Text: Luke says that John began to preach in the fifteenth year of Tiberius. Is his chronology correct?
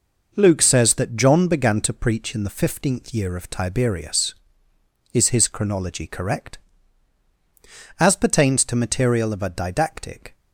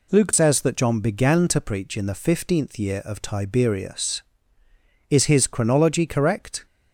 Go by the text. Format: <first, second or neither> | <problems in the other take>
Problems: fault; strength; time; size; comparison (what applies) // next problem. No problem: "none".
second | goes on to say "As pertains to material of a didactic"; strong; from 8.0 s on; 2.3 s long